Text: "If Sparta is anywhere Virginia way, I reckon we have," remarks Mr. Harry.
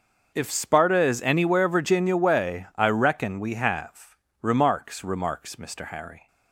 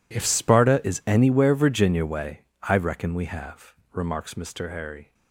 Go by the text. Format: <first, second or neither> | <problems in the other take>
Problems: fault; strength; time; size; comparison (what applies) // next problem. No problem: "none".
second | starts louder than the rest; noticeable; until 1.3 s; 6 dB // says "remarks" twice; at 5.0 s